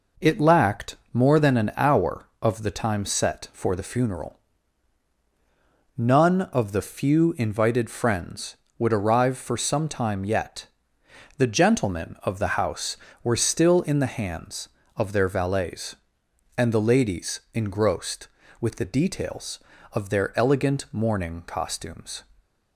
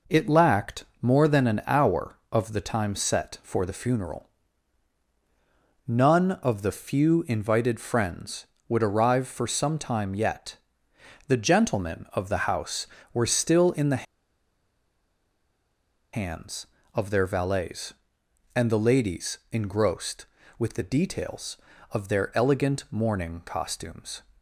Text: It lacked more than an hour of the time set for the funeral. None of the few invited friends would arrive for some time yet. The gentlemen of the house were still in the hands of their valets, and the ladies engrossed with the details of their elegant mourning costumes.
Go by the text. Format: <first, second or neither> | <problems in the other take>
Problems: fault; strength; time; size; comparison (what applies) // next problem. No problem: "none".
first | pauses between "lacked" and "more"; slight; at 0.8 s; 0.16 s long; slight in the first // pauses between "the" and "hands"; strong; at 14.0 s; 2.0 s long